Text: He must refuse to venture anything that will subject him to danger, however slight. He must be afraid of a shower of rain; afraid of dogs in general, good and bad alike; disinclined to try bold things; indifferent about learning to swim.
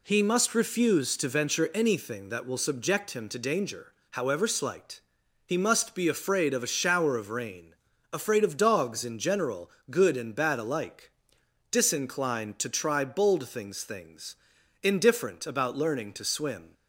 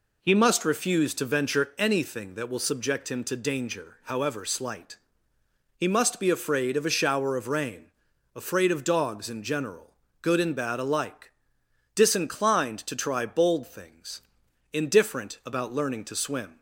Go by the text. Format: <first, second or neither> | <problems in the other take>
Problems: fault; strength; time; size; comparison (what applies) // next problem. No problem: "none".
second | says "things" twice; at 13.8 s